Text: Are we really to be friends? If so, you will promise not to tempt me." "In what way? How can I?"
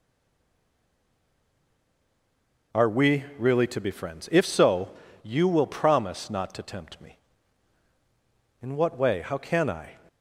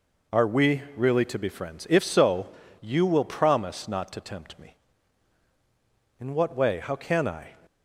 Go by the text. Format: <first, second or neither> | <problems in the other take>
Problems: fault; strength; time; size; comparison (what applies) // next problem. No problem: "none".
second | stays silent before the first word; strong; until 2.7 s; 2.7 s long